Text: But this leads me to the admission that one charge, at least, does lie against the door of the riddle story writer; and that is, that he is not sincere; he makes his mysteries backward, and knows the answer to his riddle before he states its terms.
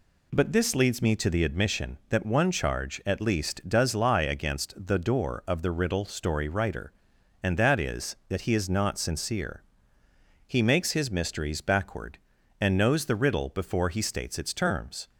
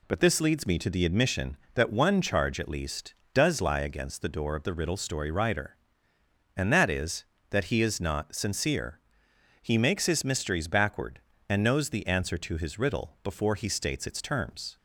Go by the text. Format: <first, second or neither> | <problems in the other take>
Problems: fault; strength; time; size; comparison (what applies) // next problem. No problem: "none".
second | skips "answer to his"; at 13.1 s